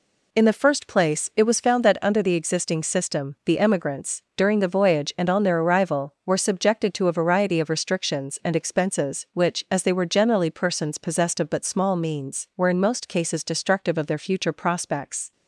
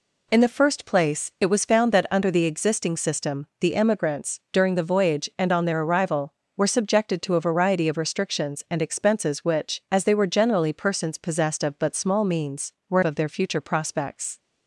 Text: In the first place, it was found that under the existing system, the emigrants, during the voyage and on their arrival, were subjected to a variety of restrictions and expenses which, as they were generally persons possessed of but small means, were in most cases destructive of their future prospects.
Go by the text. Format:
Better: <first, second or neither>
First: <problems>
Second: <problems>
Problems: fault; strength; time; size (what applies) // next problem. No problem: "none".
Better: first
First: none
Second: skips "in most cases destructive"; at 13.0 s